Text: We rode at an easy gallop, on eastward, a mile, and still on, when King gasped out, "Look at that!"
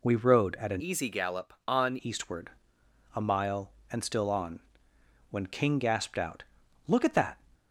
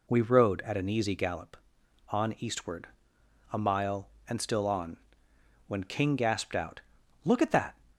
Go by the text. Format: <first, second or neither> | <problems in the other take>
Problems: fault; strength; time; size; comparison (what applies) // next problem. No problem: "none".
second | changes voice from "easy" to "on"; from 0.8 to 1.9 s; 1.1 s long